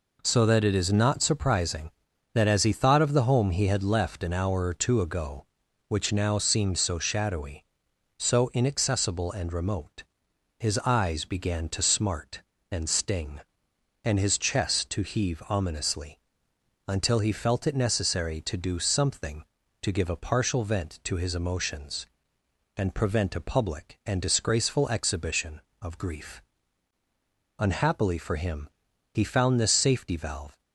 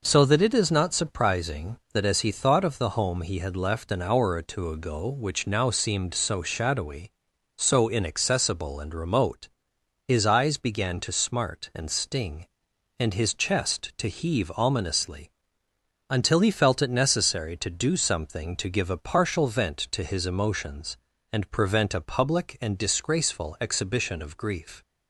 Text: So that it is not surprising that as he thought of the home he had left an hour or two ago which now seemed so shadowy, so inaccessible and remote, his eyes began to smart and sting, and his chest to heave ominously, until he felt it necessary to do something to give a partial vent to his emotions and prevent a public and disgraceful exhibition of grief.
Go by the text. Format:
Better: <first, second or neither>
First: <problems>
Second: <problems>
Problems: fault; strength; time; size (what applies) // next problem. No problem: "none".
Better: second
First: goes on to say "Unhappily for him he found this safety valve"; strong; from 27.5 s on; 3.0 s long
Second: none